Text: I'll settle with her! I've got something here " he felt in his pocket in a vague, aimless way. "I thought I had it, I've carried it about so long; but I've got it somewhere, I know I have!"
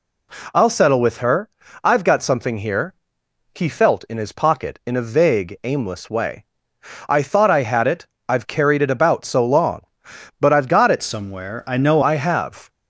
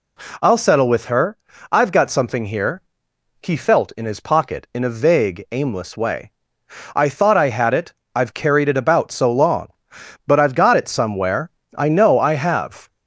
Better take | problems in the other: second | changes voice from "somewhere" to "know"; from 11.0 to 11.9 s; 0.9 s long

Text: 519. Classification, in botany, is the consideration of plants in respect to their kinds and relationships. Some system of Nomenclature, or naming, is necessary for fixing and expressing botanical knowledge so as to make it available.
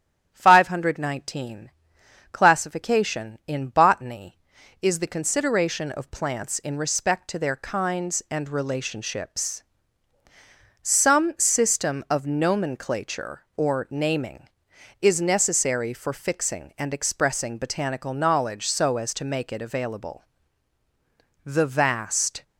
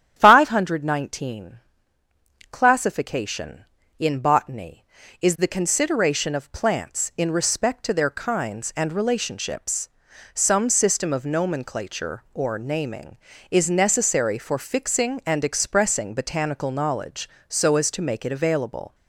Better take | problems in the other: second | starts louder than the rest; strong; until 1.3 s; 10 dB; strong in the second // goes on to say "The vast"; noticeable; from 21.4 s on; 0.98 s long

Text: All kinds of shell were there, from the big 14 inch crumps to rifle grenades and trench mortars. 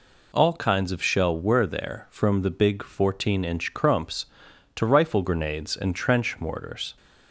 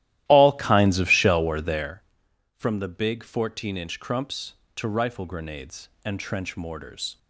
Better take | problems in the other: first | starts louder than the rest; strong; until 2.0 s; 14 dB

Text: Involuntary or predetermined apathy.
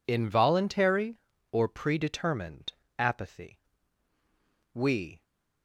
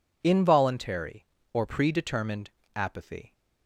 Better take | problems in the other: second | pauses between "predetermined" and "apathy"; slight; at 2.7 s; 0.26 s long; slight in the second // goes on to say "We"; slight; from 4.7 s on; 0.48 s long

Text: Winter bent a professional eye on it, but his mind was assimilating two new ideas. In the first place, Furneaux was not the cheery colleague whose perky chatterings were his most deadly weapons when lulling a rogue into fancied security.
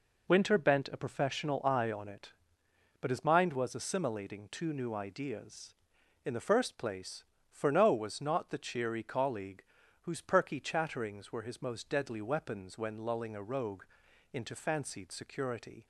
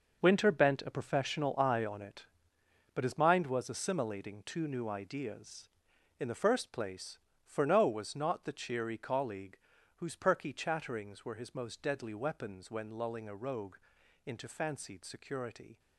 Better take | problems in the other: first | gets quieter; strong; throughout; 11 dB // pauses between "colleague" and "whose"; at 9.5 s; 0.40 s long; also in the first // pauses between "rogue" and "into"; noticeable; at 13.7 s; 0.48 s long; noticeable in the first

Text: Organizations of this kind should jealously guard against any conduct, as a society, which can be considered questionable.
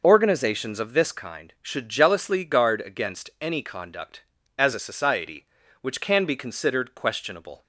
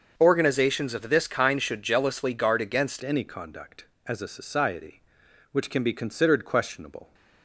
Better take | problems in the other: first | starts louder than the rest; until 1.1 s; 6.5 dB // changes voice at "any"; from 3.0 s on; 4.1 s long

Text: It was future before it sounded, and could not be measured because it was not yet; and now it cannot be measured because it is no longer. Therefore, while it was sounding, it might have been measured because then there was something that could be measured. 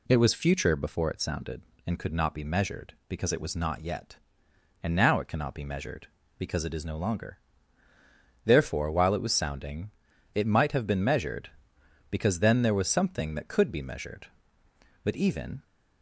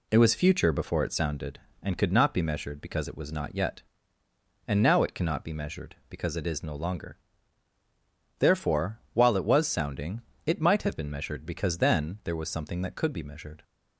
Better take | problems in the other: second | goes on to say "But even"; from 15.0 s on; 0.60 s long

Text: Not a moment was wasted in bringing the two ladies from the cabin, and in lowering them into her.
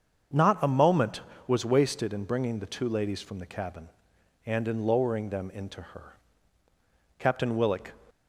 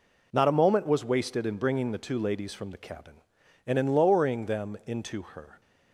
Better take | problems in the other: second | starts louder than the rest; until 1.6 s; 7 dB // goes on to say "Captain Willock"; noticeable; from 7.1 s on; 0.74 s long

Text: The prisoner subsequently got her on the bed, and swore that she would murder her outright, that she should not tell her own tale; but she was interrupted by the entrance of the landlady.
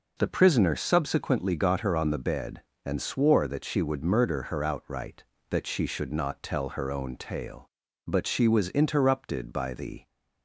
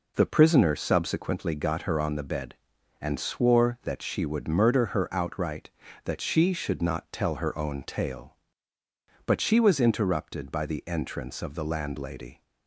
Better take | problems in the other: second | stops before "entrance of the landlady"; at 10.0 s

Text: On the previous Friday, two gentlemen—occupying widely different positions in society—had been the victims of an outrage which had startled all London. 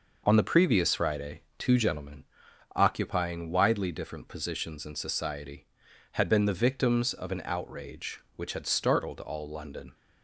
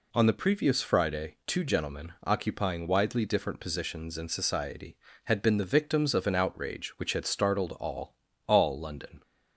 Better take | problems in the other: first | says "all" twice; at 8.4 s

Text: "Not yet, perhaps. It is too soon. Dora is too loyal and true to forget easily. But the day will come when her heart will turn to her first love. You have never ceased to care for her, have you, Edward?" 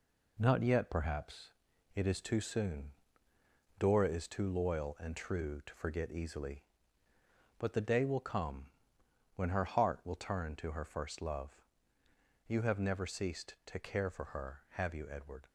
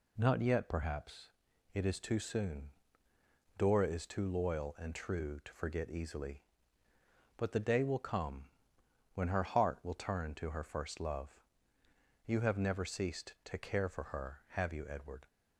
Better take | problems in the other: second | gets quieter; noticeable; throughout; 6 dB // pauses between "come" and "when"; noticeable; at 8.6 s; 0.68 s long; noticeable in the second

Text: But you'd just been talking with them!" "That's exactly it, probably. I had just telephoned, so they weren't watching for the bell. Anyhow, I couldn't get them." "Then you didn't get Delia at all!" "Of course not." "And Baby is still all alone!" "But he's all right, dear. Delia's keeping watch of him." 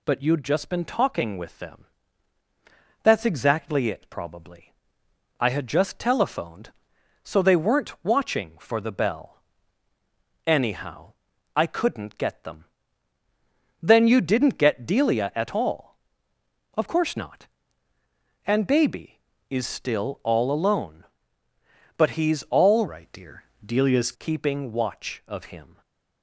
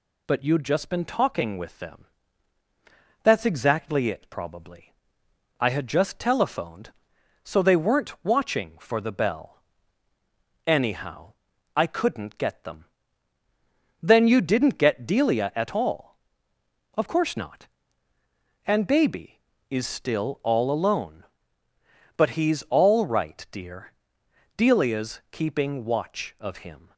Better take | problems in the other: second | changes voice from "right" to "Delia's"; from 22.8 to 24.1 s; 1.3 s long // stays silent after the last word; slight; from 25.7 s on; 0.5 s long

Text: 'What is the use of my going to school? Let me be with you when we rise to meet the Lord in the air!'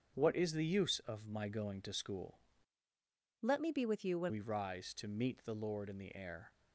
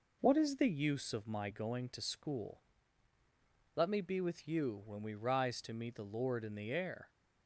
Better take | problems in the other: second | starts louder than the rest; strong; until 1.1 s; 7 dB // changes voice from "Let" to "when"; from 3.4 to 4.3 s; 0.9 s long

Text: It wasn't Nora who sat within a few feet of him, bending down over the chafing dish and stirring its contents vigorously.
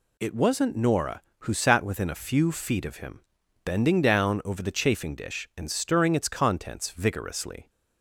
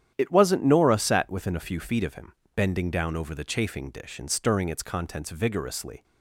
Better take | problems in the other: first | starts louder than the rest; strong; until 1.1 s; 10 dB // skips "who"; at 0.9 s

